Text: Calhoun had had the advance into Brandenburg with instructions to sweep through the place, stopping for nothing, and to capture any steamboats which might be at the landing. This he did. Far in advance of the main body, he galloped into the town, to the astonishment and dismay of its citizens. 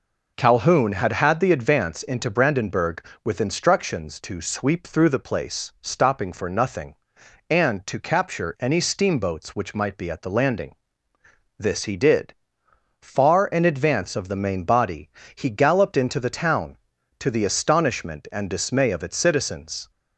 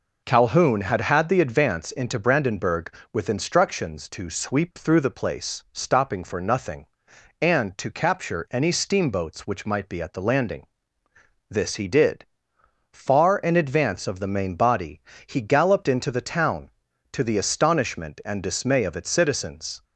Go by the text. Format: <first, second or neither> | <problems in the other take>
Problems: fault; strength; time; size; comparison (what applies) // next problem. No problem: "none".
neither | none